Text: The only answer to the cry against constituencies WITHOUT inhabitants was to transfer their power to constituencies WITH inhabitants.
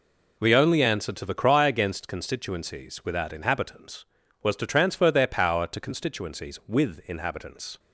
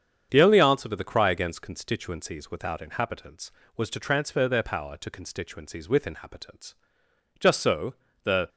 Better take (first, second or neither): first